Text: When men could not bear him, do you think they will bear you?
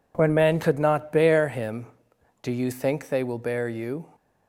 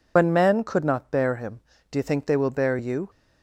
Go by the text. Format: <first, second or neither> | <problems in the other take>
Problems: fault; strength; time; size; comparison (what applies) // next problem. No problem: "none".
first | loses the start of "When"; at 0.1 s; 80 ms